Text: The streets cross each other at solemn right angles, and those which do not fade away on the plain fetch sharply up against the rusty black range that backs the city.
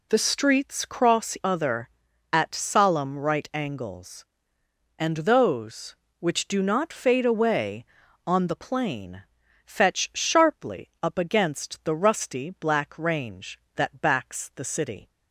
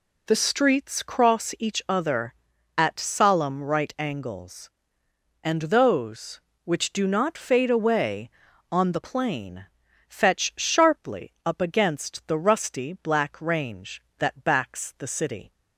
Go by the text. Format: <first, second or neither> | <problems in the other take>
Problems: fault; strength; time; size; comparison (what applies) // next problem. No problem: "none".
second | skips "each"; at 1.3 s // pauses between "plain" and "fetch"; noticeable; at 9.2 s; 0.46 s long; noticeable in the second